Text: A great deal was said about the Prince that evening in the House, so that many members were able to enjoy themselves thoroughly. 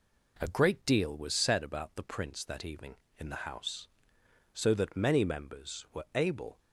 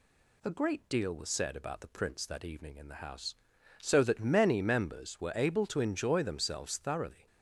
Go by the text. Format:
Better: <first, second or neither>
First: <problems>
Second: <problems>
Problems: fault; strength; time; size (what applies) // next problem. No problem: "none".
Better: second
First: stops before "to enjoy themselves thoroughly"; at 6.5 s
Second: none